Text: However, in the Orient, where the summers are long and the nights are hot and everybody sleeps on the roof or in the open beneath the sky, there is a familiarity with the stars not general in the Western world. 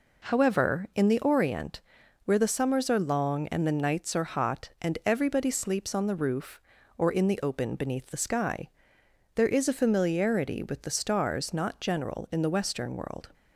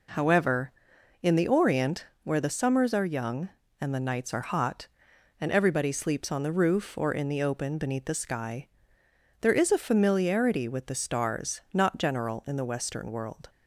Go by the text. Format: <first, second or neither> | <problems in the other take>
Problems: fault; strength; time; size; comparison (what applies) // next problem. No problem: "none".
first | says "young" for "long"; at 3.0 s